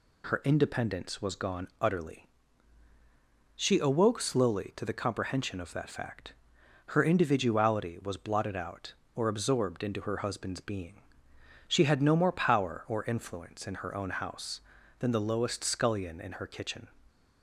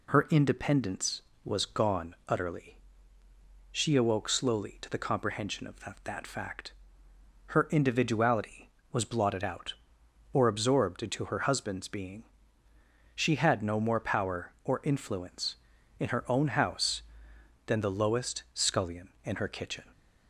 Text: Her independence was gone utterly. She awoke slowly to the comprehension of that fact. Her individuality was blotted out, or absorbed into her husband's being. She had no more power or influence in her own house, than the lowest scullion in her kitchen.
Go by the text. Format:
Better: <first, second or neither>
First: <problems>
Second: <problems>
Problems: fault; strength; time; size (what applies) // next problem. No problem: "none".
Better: first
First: none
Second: says "that" twice; at 6.0 s